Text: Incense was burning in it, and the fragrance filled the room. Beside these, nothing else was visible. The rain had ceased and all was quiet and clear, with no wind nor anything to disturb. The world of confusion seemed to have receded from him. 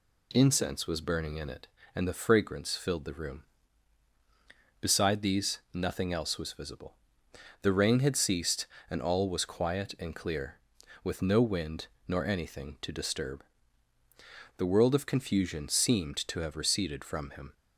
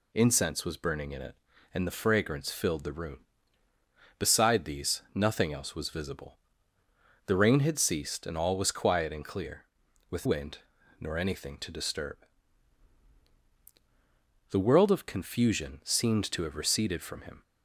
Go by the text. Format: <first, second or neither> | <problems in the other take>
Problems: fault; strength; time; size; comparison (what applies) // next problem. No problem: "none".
first | skips "no"; at 10.2 s // pauses between "wind" and "nor"; at 10.5 s; 0.40 s long; slight in the first